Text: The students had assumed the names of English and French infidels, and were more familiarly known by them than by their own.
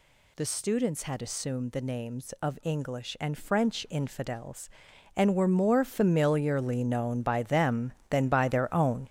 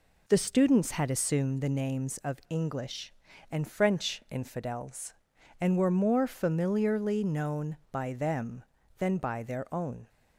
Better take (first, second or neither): second